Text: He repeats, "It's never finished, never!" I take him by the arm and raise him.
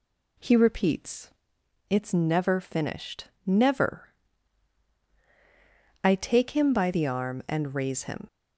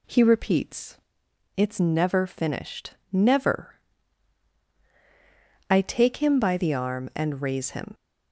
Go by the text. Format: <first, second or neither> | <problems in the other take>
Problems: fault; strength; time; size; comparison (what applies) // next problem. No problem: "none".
neither | none